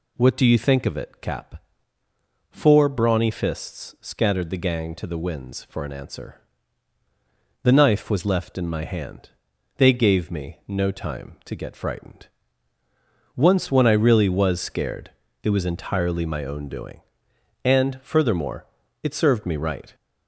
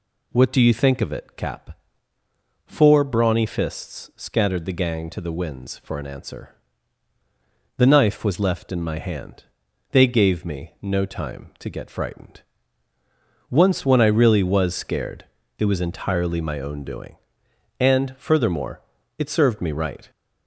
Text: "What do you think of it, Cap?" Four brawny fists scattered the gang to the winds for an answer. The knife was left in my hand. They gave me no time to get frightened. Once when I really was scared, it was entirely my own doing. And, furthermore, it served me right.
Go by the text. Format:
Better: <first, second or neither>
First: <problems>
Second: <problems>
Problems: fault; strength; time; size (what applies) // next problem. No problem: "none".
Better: neither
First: none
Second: none